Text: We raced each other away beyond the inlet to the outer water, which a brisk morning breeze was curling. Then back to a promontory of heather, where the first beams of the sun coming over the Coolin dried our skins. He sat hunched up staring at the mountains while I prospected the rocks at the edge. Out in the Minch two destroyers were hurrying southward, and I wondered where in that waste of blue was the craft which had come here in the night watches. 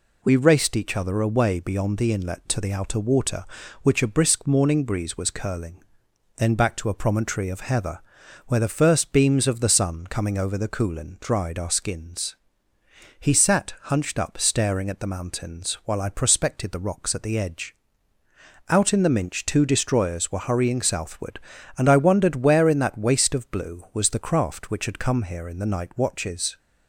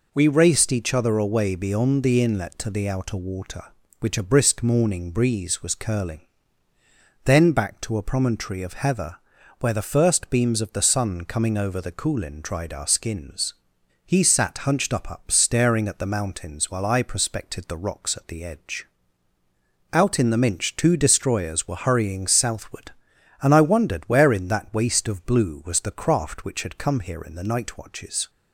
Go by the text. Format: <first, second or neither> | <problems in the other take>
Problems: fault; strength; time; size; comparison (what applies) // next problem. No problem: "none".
first | says "up" twice; at 15.1 s